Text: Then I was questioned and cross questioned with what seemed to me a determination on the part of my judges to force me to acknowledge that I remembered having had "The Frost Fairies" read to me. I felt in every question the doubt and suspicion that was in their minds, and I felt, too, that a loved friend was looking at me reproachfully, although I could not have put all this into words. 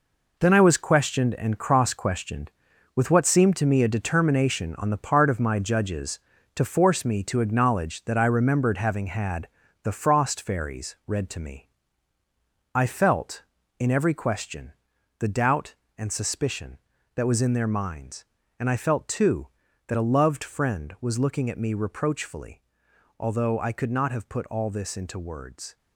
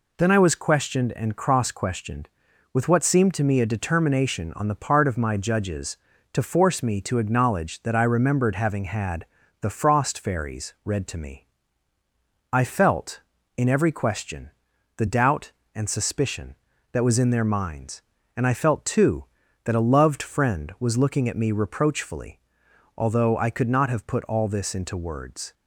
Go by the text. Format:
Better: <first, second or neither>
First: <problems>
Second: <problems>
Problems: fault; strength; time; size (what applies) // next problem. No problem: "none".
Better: second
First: gets quieter; strong; throughout; 9 dB // pauses between "had" and "The"; slight; at 9.4 s; 0.34 s long // pauses between "question" and "the"; noticeable; at 14.7 s; 0.46 s long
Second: pauses between "had" and "The"; slight; at 9.2 s; 0.34 s long // pauses between "question" and "the"; noticeable; at 14.5 s; 0.46 s long